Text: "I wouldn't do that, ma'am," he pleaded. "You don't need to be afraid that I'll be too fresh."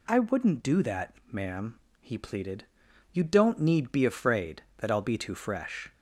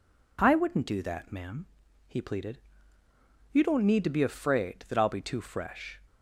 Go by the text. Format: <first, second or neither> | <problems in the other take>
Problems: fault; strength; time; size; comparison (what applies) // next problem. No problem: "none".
second | skips "to"; at 3.9 s